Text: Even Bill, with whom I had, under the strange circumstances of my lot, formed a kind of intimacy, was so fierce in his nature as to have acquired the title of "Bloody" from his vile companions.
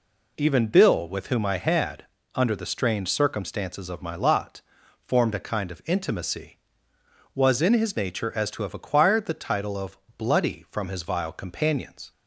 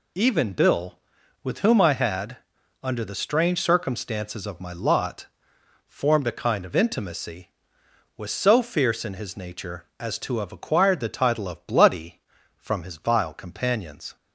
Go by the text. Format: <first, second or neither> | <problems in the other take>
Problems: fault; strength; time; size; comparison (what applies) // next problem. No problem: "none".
second | skips "so fierce"; at 7.6 s // pauses between "of" and "Bloody"; slight; at 9.9 s; 0.20 s long